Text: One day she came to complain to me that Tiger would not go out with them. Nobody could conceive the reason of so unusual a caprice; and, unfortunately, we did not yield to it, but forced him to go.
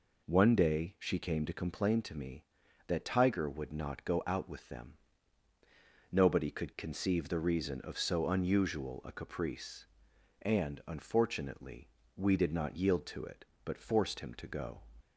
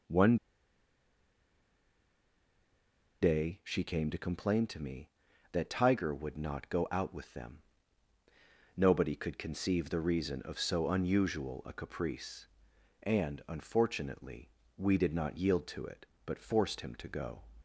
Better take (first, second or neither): first